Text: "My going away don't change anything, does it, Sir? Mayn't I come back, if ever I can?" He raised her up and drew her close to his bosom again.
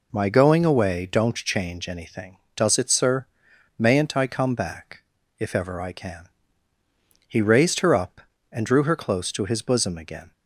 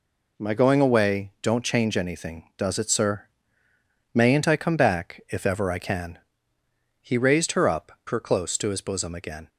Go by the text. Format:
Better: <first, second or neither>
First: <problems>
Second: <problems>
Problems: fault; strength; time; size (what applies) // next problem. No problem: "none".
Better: first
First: none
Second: skips "and drew"; at 8.0 s